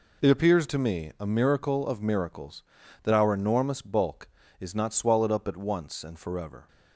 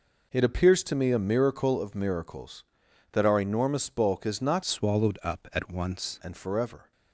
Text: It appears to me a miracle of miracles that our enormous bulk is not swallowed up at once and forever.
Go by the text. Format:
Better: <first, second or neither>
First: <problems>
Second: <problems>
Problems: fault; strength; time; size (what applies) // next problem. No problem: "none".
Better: first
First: none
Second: changes voice from "swallowed" to "once"; from 4.6 to 6.1 s; 1.5 s long